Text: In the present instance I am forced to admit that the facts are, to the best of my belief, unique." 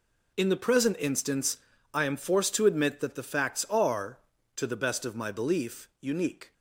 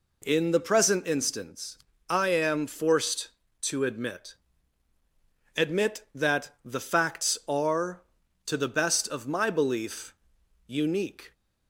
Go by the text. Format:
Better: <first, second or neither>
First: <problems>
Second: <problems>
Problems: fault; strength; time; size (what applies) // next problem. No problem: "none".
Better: first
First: pauses between "instance" and "I"; slight; at 1.5 s; 0.36 s long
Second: pauses between "instance" and "I"; slight; at 1.7 s; 0.32 s long // says "admit" twice; at 5.5 s